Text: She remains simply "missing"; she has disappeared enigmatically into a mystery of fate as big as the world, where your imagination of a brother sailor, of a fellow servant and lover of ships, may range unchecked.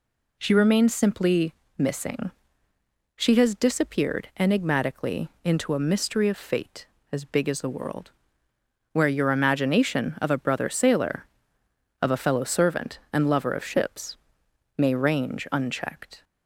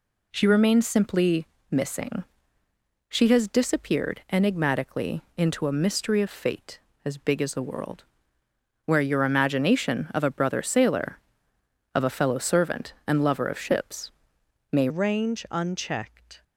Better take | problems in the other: first | pauses between "simply" and "missing"; slight; at 1.4 s; 0.24 s long; slight in the first // pauses between "enigmatically" and "into"; slight; at 5.1 s; 0.16 s long; slight in the first // changes voice at "range"; from 14.8 s on; 1.6 s long

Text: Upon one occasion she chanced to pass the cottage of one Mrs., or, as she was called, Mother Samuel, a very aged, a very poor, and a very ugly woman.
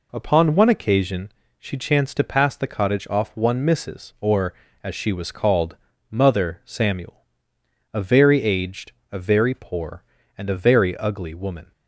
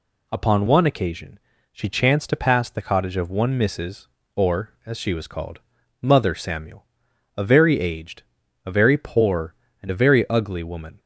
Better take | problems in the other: second | pauses between "occasion" and "she"; slight; at 1.3 s; 0.28 s long; slight in the second // says "off" for "of"; at 3.0 s

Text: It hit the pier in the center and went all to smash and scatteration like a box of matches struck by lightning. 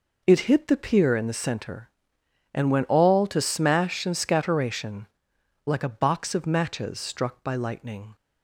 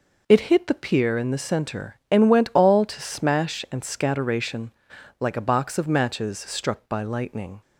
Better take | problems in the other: neither | pauses between "scatteration" and "like"; noticeable; the same in both

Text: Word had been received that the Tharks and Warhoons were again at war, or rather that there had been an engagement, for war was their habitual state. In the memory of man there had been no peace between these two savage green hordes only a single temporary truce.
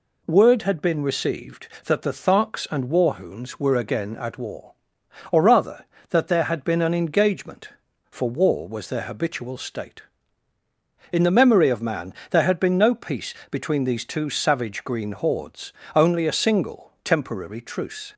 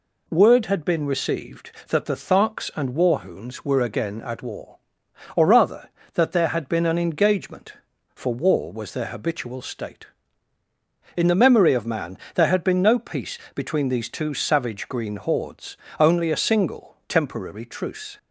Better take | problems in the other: neither | pauses between "man" and "there"; slight; the same in both // pauses between "peace" and "between"; slight; the same in both // pauses between "hordes" and "only"; slight; the same in both

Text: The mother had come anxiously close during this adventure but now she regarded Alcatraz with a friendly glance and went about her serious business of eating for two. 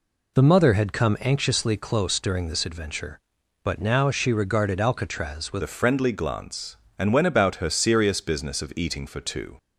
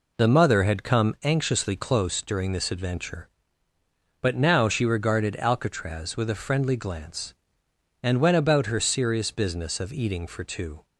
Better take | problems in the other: second | changes voice at "a"; from 5.6 s on; 3.9 s long

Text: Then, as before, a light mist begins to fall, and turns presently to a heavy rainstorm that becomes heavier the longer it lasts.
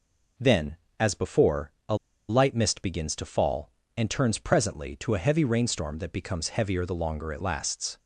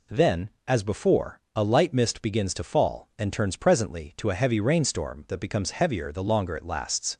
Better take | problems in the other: second | pauses between "a" and "light"; slight; at 1.9 s; 0.34 s long

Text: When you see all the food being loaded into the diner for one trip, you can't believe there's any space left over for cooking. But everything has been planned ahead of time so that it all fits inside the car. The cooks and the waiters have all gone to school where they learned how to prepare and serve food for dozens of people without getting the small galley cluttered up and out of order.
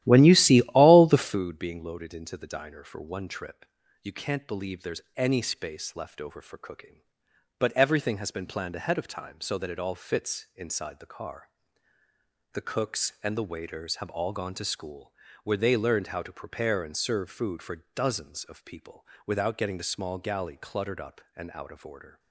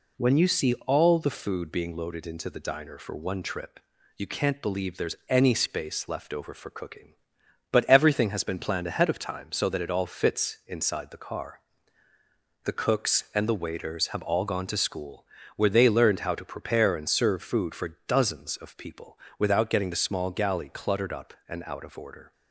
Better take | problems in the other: second | starts louder than the rest; strong; until 1.5 s; 13.5 dB // pauses between "school" and "where"; slight; at 15.1 s; 0.30 s long; slight in the second // pauses between "people" and "without"; slight; at 19.0 s; 0.22 s long; slight in the second

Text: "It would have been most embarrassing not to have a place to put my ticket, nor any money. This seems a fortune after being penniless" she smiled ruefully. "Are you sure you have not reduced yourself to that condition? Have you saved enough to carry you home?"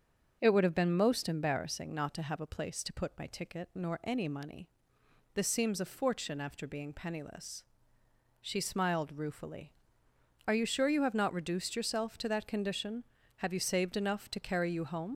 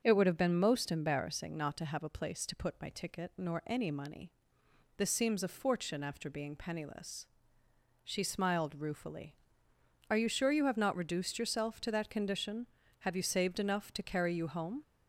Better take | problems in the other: second | starts louder than the rest; until 1.4 s; 6.5 dB; also in the second // pauses between "penniless" and "she"; noticeable; at 7.6 s; 0.74 s long; noticeable in the second // leaves "home" unfinished; at 15.1 s; 45 ms

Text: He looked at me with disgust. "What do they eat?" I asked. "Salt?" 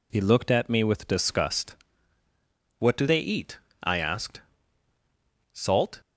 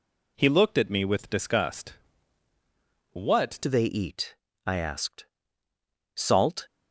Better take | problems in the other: first | changes voice at "do"; from 3.6 s on; 3.0 s long

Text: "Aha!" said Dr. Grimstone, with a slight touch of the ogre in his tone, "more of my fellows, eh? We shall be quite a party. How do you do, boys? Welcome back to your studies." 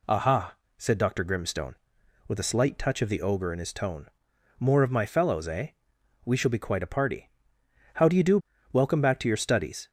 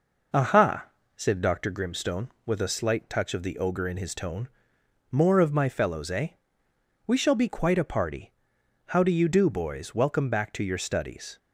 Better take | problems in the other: second | skips "boys"; at 8.5 s

